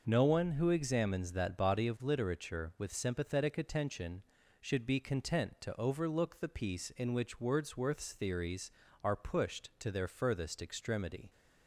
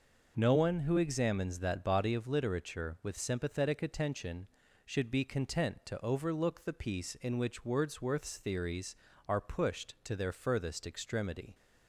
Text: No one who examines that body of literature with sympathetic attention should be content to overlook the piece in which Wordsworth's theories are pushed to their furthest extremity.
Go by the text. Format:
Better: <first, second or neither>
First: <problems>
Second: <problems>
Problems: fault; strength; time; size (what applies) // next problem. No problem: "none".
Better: neither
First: none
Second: none